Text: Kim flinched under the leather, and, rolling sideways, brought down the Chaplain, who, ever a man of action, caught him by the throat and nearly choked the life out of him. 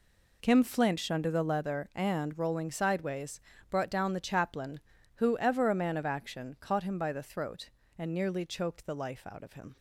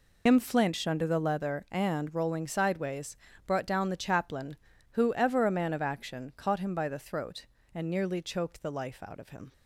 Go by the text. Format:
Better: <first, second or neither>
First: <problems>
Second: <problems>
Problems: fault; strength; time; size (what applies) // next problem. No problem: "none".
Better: first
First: none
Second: loses the start of "Kim"; at 0.2 s; 75 ms